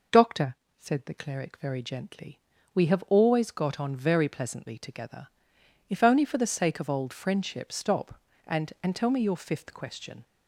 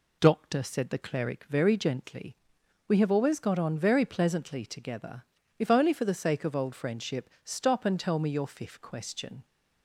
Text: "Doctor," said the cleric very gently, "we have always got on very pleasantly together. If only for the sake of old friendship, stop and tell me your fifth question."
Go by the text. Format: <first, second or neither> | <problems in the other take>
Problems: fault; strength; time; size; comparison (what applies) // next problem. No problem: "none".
second | says "and" twice; at 8.8 s